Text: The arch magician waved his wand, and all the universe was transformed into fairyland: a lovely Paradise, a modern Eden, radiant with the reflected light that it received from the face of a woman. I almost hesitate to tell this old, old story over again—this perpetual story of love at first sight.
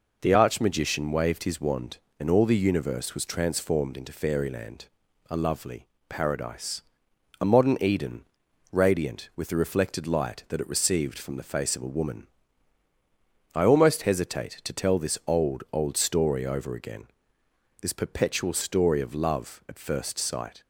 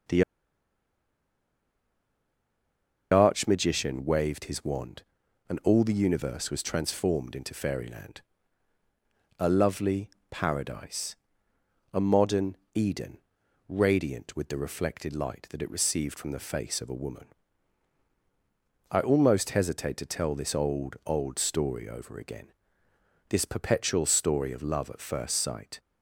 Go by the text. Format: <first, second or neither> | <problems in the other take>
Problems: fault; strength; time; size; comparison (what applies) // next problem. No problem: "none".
first | pauses between "The" and "arch"; strong; at 0.2 s; 2.8 s long // pauses between "lovely" and "Paradise"; slight; at 10.0 s; 0.22 s long; slight in the first // pauses between "modern" and "Eden"; slight; at 12.5 s; 0.16 s long